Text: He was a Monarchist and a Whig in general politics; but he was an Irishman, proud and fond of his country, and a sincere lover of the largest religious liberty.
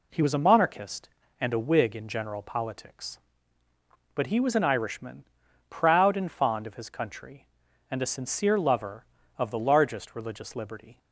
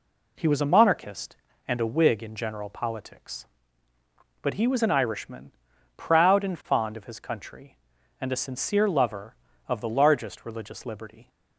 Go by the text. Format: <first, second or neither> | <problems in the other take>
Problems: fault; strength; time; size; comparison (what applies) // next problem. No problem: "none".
neither | none